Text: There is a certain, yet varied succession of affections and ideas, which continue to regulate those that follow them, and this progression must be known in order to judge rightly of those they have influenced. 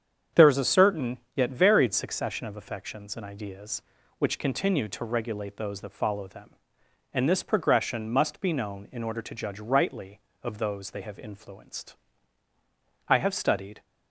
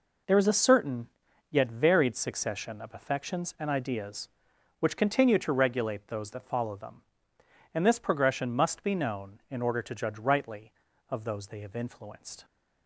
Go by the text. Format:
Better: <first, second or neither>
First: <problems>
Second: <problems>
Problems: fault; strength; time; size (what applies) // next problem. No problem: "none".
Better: second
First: starts louder than the rest; strong; until 1.5 s; 8 dB // goes on to say "I have studied"; noticeable; from 13.0 s on; 0.76 s long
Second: none